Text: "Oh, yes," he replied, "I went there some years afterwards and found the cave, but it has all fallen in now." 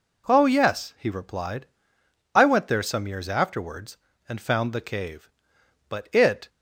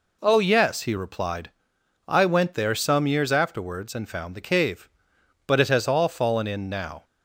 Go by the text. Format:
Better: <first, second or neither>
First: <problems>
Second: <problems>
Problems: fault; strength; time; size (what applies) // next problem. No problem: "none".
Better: second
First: stops before "has all fallen in now"; at 6.4 s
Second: none